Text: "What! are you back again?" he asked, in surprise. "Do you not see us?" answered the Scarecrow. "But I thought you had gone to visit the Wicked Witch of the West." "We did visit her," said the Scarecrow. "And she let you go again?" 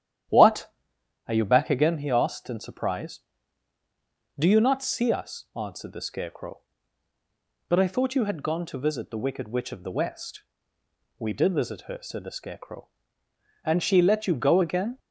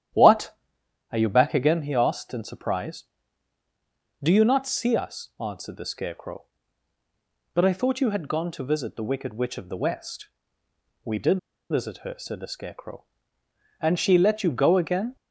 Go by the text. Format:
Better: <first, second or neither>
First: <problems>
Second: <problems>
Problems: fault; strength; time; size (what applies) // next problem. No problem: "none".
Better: first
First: starts louder than the rest; strong; until 1.8 s; 10.5 dB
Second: starts louder than the rest; strong; until 1.7 s; 10.5 dB // pauses between "did" and "visit"; slight; at 11.3 s; 0.31 s long